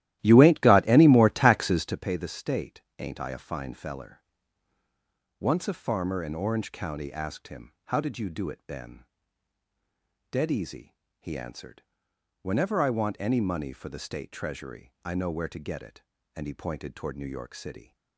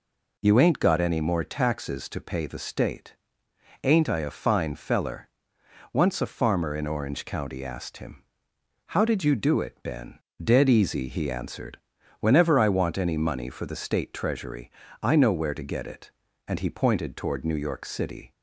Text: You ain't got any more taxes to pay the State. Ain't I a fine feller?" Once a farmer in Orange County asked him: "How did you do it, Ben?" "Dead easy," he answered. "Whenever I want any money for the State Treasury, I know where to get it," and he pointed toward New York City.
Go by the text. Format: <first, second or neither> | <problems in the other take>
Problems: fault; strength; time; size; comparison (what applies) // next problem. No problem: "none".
second | starts louder than the rest; strong; until 2.0 s; 14 dB